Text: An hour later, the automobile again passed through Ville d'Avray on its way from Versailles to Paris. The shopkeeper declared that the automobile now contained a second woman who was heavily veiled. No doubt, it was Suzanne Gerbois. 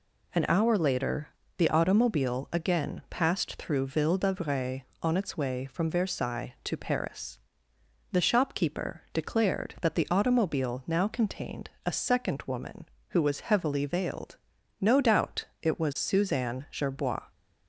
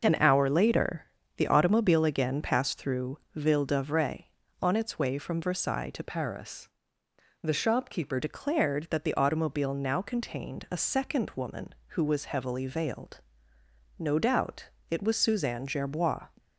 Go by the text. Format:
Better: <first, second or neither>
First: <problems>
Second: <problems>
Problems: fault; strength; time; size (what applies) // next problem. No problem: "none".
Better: first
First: none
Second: pauses between "through" and "Ville"; slight; at 3.1 s; 0.16 s long // changes voice from "Paris" to "shopkeeper"; from 6.0 to 8.1 s; 2.1 s long